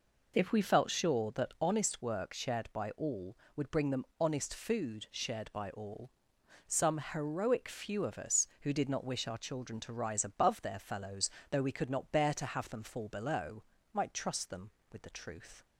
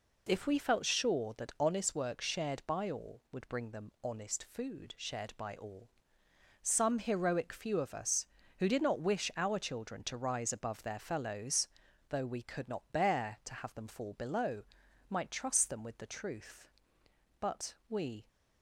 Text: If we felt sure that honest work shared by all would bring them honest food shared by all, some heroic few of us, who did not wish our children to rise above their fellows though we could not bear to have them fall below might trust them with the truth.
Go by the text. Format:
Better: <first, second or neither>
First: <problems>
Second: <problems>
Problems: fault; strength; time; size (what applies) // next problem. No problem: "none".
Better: first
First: pauses between "fellows" and "though"; slight; at 11.2 s; 0.22 s long // pauses between "below" and "might"; slight; at 13.6 s; 0.30 s long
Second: pauses between "fellows" and "though"; at 11.6 s; 0.42 s long // pauses between "below" and "might"; noticeable; at 14.6 s; 0.46 s long // goes on to say "But we"; noticeable; from 17.3 s on; 0.88 s long